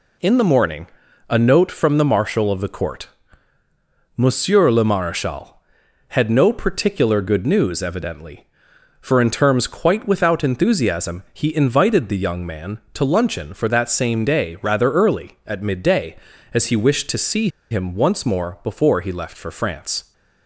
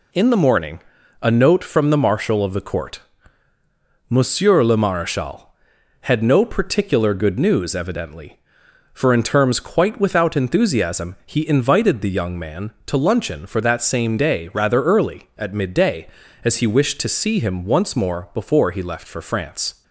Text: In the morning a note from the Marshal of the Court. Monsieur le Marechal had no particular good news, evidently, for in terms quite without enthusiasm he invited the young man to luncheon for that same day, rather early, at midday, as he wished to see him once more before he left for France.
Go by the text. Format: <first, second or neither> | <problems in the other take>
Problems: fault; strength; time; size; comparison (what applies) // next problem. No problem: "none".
second | pauses between "morning" and "a"; at 0.8 s; 0.42 s long; also in the second // pauses between "see" and "him"; slight; at 17.4 s; 0.22 s long